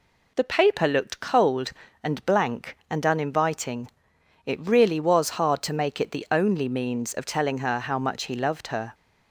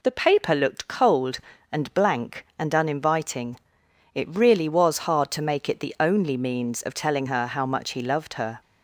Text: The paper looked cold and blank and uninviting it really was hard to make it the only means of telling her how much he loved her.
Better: neither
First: pauses between "uninviting" and "it"; noticeable; at 3.9 s; 0.56 s long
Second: pauses between "uninviting" and "it"; noticeable; at 3.5 s; 0.56 s long

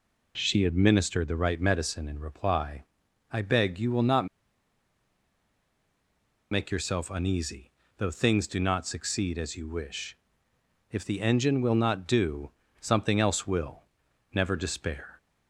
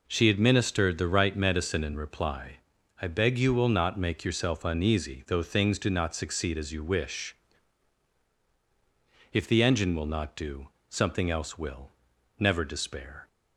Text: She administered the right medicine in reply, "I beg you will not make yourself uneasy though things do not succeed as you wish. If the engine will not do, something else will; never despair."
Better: second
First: pauses between "not" and "make"; strong; at 4.2 s; 2.2 s long // pauses between "uneasy" and "though"; slight; at 7.7 s; 0.24 s long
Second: none

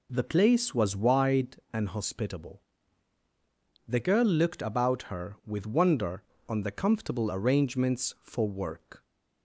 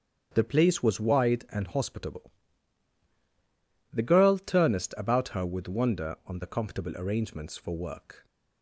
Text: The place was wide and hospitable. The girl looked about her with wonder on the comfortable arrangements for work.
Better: first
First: none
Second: starts louder than the rest; strong; until 1.3 s; 7 dB // says "turnest" for "looked"; at 4.3 s

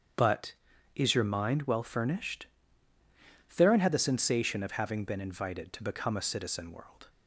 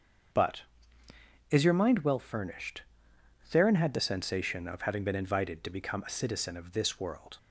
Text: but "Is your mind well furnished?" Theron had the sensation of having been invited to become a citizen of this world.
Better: second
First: starts louder than the rest; strong; until 1.5 s; 8 dB // skips "of this"; at 6.7 s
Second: starts louder than the rest; until 2.2 s; 7 dB

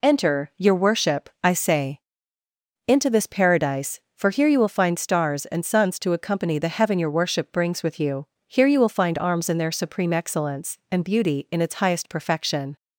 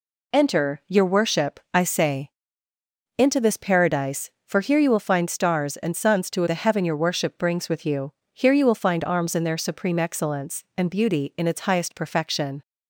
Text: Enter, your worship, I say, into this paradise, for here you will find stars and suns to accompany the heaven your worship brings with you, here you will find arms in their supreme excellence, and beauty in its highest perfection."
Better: first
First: none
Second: skips "accompany"; at 6.4 s

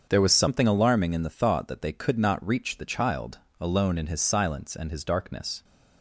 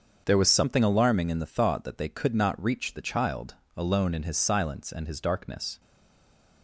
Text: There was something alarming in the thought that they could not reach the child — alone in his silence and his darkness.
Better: first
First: starts louder than the rest; until 1.1 s; 7 dB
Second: starts louder than the rest; until 1.2 s; 7 dB // stays silent after the last word; slight; from 5.7 s on; 0.9 s long

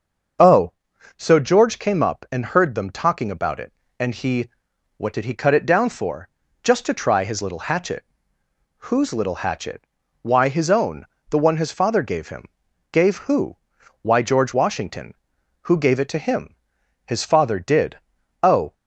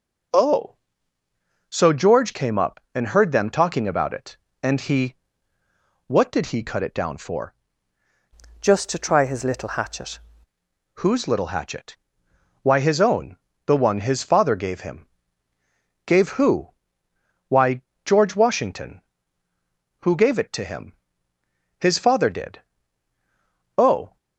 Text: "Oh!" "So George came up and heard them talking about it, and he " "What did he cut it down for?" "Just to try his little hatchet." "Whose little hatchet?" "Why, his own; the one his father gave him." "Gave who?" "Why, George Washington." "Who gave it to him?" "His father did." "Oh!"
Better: first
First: starts louder than the rest; noticeable; until 1.8 s; 6 dB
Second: starts louder than the rest; until 2.2 s; 6.5 dB // changes voice from "Just" to "hatchet"; from 8.6 to 10.1 s; 1.5 s long

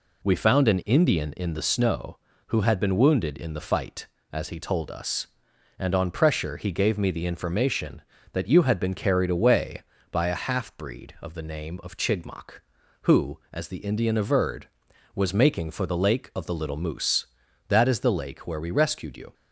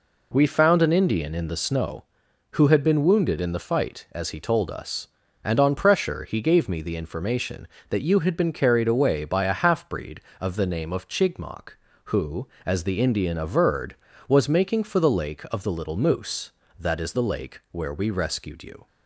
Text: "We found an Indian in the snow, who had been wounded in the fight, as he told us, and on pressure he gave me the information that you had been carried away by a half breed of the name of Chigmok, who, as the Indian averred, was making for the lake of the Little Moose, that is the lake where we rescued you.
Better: neither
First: none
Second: none

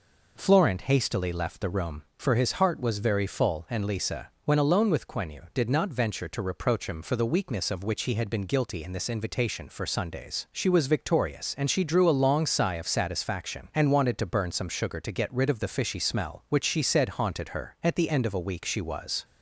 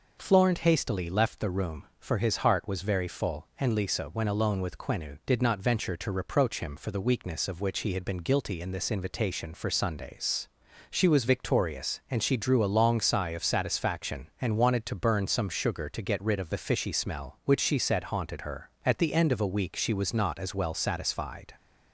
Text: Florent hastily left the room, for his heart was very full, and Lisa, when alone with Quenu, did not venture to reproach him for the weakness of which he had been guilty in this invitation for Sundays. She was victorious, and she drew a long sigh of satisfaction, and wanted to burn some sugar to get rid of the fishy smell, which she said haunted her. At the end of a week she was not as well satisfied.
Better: second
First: stops before "not as well satisfied"; at 19.2 s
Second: none

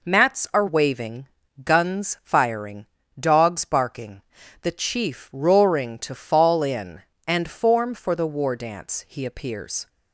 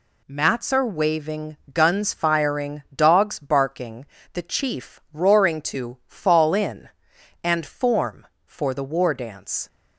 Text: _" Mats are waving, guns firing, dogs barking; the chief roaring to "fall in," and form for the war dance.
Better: second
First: goes on to say "He appears"; noticeable; from 9.0 s on; 0.80 s long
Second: none

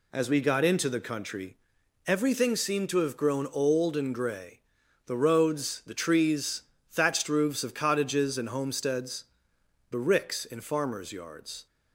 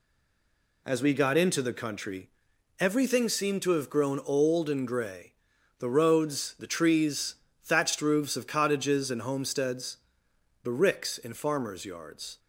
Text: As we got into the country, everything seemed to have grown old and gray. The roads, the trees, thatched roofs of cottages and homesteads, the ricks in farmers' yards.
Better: first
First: none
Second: stays silent before the first word; slight; until 0.8 s; 0.8 s long

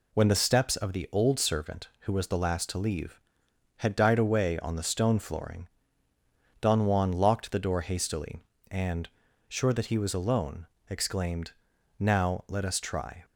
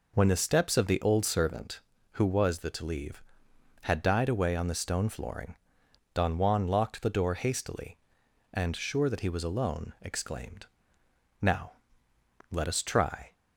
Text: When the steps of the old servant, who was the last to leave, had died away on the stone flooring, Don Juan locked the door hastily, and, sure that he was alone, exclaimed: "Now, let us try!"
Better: first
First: none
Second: skips "last"; at 2.7 s

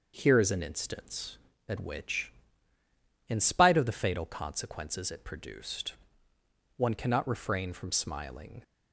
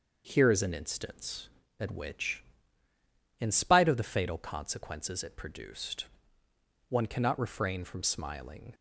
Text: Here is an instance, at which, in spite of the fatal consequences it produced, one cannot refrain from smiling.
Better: neither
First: none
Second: none

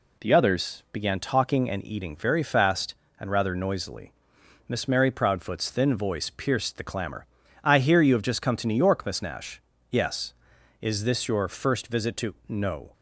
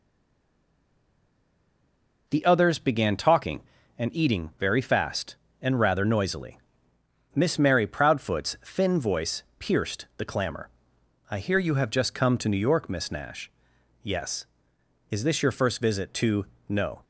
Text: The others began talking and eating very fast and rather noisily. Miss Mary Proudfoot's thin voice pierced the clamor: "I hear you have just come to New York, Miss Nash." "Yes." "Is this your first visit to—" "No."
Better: first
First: none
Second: stays silent before the first word; until 2.2 s; 2.2 s long // pauses between "voice" and "pierced"; slight; at 9.4 s; 0.16 s long

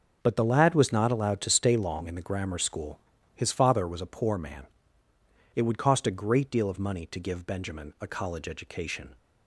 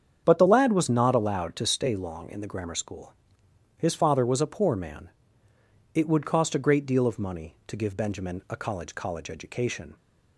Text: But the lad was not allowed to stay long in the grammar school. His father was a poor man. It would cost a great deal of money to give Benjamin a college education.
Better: first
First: none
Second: starts louder than the rest; strong; until 1.2 s; 8 dB // says "college" twice; at 8.9 s

